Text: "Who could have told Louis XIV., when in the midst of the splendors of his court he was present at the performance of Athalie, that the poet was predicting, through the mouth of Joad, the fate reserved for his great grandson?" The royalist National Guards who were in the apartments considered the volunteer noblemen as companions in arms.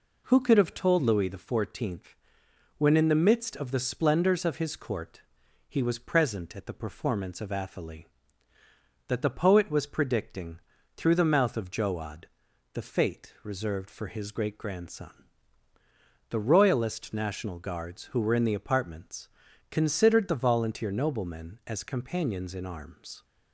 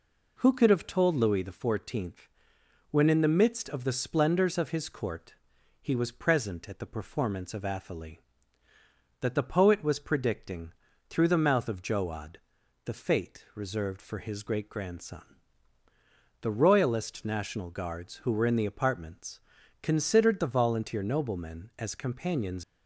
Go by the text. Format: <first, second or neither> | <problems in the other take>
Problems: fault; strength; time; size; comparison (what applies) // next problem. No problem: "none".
first | pauses between "court" and "he"; noticeable; at 5.3 s; 0.48 s long; noticeable in the first // pauses between "apartments" and "considered"; at 19.3 s; 0.44 s long; also in the first // stops before "in arms"; at 22.6 s